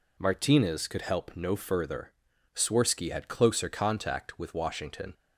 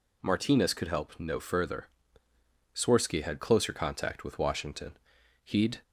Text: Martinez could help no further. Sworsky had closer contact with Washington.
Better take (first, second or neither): first